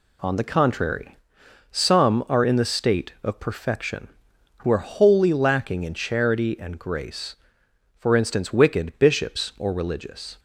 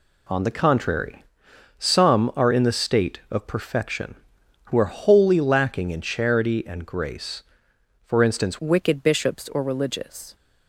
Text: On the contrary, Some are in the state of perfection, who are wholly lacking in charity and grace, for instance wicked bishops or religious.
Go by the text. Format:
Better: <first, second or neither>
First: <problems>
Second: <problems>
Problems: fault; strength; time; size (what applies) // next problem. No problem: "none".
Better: first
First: none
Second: changes voice at "wicked"; from 8.5 s on; 1.8 s long